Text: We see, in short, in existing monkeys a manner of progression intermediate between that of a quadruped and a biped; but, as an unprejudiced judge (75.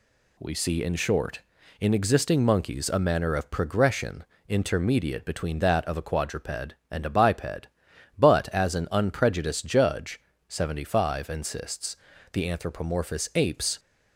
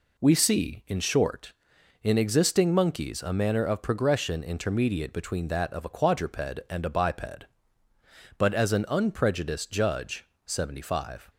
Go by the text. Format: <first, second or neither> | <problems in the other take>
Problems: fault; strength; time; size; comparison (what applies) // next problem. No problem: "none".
second | pauses between "progression" and "intermediate"; slight; at 4.2 s; 0.24 s long // goes on to say "insists the anthropomorphous apes"; strong; from 11.2 s on; 2.5 s long